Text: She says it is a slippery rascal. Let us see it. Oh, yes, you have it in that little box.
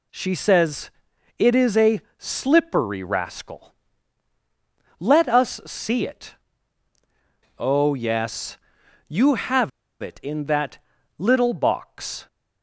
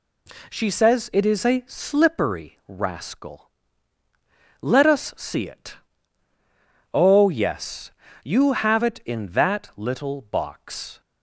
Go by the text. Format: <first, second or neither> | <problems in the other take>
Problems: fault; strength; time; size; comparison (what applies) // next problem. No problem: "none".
second | pauses between "says" and "it"; noticeable; at 0.9 s; 0.48 s long // pauses between "a" and "slippery"; slight; at 2.0 s; 0.18 s long // pauses between "have" and "it"; slight; at 9.7 s; 0.30 s long // pauses between "that" and "little"; at 10.7 s; 0.38 s long